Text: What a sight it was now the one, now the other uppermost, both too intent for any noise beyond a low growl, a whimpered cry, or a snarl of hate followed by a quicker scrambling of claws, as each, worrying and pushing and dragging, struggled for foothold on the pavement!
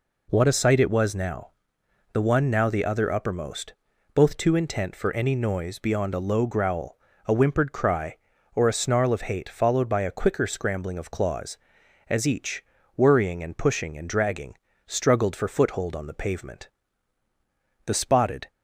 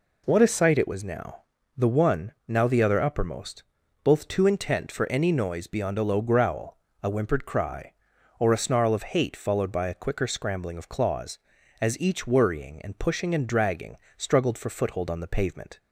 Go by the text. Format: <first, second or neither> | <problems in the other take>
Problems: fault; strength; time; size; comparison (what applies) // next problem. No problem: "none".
second | pauses between "now" and "the"; noticeable; at 1.4 s; 0.64 s long; slight in the second // goes on to say "The spotted"; noticeable; from 17.8 s on; 0.64 s long